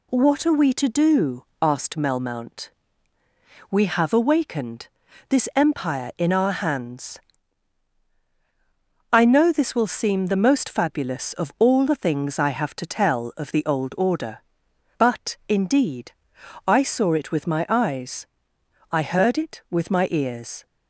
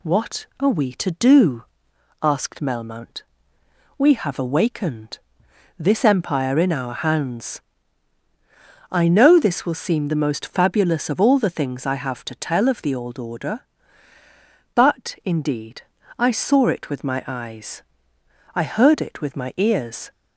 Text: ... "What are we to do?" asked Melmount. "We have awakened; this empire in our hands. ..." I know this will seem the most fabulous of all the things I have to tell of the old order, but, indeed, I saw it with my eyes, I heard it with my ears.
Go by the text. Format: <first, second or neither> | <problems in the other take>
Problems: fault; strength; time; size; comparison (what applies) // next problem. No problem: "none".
neither | none